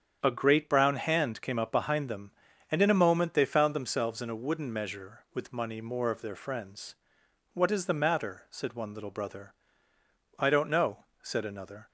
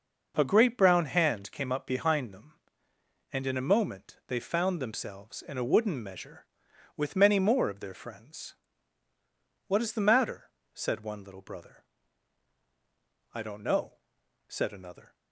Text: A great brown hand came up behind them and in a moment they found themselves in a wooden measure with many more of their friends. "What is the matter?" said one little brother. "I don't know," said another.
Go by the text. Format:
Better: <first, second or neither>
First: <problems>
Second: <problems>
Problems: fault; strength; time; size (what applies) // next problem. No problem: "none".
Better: second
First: starts louder than the rest; strong; until 1.2 s; 8 dB // says "money" for "many"; at 5.5 s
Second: none